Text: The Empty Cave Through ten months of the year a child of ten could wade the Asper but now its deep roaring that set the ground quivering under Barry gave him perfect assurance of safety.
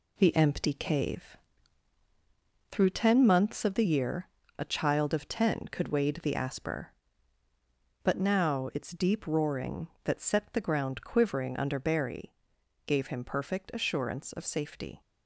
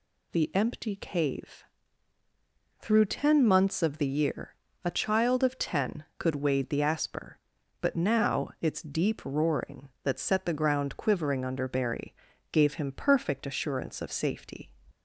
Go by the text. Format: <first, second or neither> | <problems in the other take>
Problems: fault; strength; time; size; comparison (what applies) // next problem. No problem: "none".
second | gets quieter; noticeable; throughout; 6 dB // pauses between "Cave" and "Through"; strong; at 1.3 s; 1.3 s long; also in the second // pauses between "year" and "a"; slight; at 4.2 s; 0.28 s long; slight in the second // pauses between "Barry" and "gave"; noticeable; at 12.3 s; 0.52 s long; also in the second